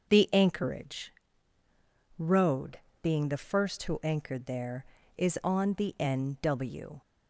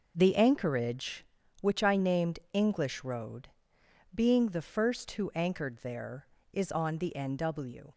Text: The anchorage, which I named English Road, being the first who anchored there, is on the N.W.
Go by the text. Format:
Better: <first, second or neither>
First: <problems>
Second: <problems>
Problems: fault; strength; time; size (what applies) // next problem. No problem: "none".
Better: second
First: skips "which I named English"; at 1.6 s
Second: none